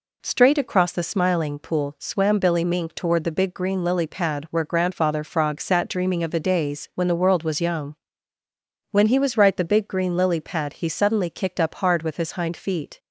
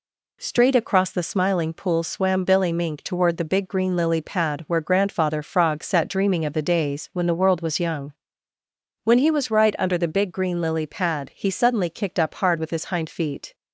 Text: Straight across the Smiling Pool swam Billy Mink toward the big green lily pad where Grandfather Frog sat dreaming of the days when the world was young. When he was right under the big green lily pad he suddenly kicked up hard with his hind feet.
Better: second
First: skips "under"; at 9.5 s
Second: none

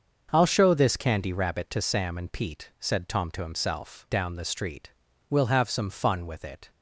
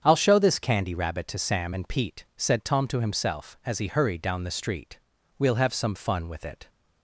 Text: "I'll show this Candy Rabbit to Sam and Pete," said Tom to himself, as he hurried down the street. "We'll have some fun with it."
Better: second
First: starts louder than the rest; until 1.3 s; 6.5 dB // skips "as he hurried"; at 4.0 s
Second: starts louder than the rest; strong; until 1.0 s; 7.5 dB

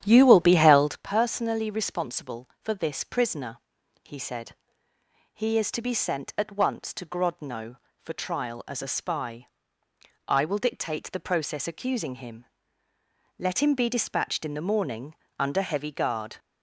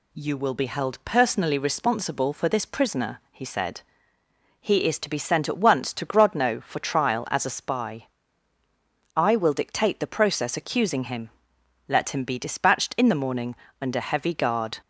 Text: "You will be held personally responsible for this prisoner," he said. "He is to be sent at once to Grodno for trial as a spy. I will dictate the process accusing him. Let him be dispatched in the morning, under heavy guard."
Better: second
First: starts louder than the rest; strong; until 1.1 s; 10.5 dB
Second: none

